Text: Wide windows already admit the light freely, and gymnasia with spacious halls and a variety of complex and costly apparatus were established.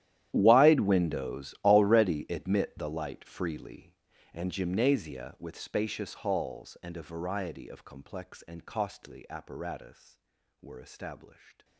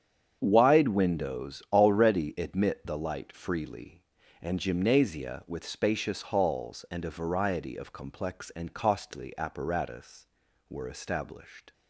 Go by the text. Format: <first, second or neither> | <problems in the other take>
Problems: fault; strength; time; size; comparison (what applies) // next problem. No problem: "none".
second | gets quieter; strong; throughout; 21 dB // starts louder than the rest; strong; until 1.3 s; 12 dB; strong in the second